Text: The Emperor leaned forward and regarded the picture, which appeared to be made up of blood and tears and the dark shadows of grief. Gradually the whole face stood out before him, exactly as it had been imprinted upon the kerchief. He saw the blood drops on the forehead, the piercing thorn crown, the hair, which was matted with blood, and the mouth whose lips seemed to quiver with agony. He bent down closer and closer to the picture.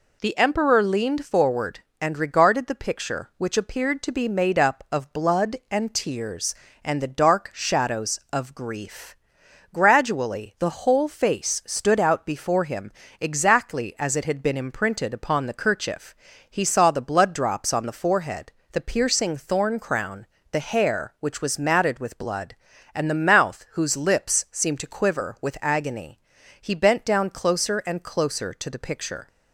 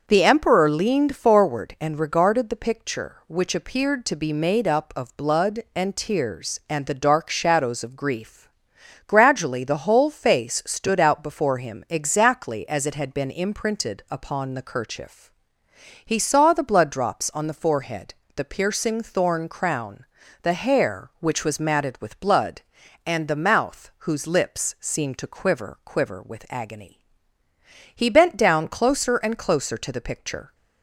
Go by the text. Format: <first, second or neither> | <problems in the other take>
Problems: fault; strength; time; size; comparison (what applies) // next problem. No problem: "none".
first | starts louder than the rest; until 1.0 s; 6.5 dB // says "quiver" twice; at 25.8 s